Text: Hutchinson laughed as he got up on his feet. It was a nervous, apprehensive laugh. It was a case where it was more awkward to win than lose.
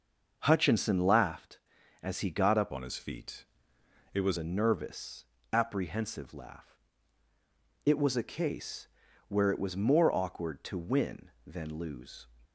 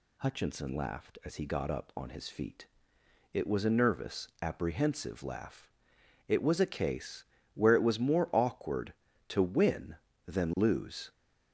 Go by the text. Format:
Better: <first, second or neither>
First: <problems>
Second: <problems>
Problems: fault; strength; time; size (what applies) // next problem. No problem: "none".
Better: second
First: starts louder than the rest; noticeable; until 1.4 s; 6 dB // changes voice from "on" to "was"; from 2.7 to 4.3 s; 1.6 s long // pauses between "case" and "where"; at 8.8 s; 0.40 s long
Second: pauses between "case" and "where"; slight; at 7.2 s; 0.28 s long